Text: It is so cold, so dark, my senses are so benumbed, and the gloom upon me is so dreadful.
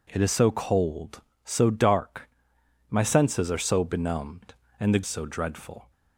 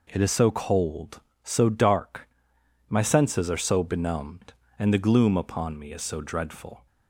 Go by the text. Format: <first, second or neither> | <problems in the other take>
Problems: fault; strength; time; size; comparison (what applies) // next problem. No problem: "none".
second | skips "gloom upon me is"; at 5.0 s